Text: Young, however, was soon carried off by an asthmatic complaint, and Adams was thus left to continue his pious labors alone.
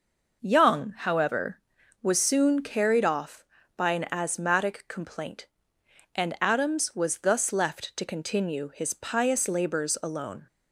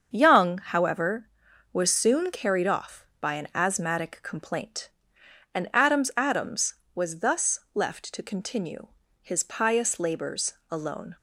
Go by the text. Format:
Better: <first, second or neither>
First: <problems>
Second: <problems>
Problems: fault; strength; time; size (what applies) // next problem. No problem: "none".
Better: first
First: none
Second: starts louder than the rest; until 1.1 s; 7 dB // says "Adams" twice; at 6.1 s // pauses between "continue" and "his"; slight; at 8.8 s; 0.34 s long // pauses between "labors" and "alone"; slight; at 10.5 s; 0.18 s long